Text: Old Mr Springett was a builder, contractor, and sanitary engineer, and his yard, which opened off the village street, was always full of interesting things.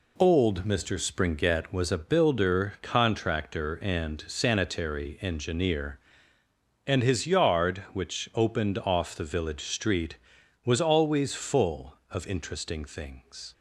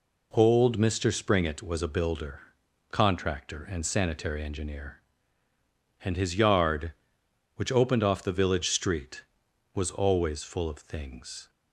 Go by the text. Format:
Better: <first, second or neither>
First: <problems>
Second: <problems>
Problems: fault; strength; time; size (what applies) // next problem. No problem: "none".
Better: first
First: none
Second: skips "interesting"; at 10.7 s